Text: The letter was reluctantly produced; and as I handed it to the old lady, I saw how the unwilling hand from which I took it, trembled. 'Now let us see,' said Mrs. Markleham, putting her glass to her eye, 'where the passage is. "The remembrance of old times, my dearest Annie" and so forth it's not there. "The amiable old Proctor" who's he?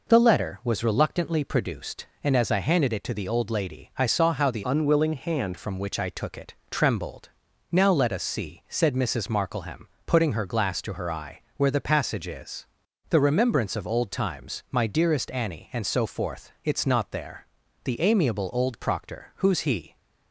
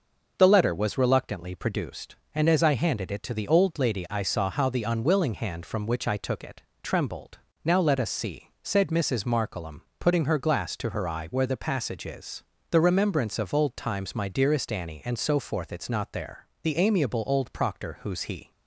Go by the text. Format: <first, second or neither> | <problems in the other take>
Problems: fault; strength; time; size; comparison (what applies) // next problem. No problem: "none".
second | changes voice from "unwilling" to "hand"; from 4.6 to 5.5 s; 0.9 s long